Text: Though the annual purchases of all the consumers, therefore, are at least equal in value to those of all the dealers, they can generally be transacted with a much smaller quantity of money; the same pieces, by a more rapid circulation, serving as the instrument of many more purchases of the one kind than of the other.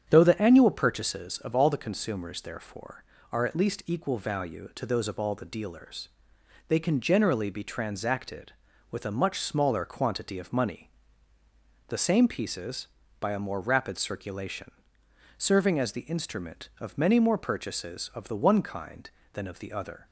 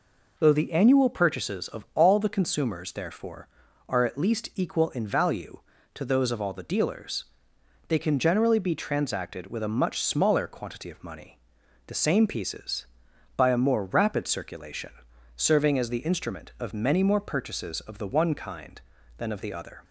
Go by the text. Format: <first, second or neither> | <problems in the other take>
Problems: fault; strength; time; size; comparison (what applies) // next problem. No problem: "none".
second | starts louder than the rest; strong; until 1.0 s; 8.5 dB // skips "in"; at 4.1 s